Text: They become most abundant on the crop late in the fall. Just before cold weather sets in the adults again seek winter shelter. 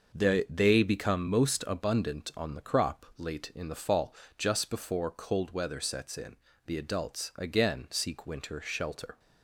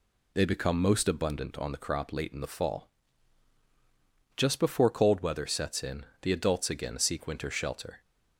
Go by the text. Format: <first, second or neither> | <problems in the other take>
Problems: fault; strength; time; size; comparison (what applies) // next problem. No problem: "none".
second | says "They" twice; at 0.4 s // pauses between "in" and "the"; slight; at 6.3 s; 0.28 s long; slight in the second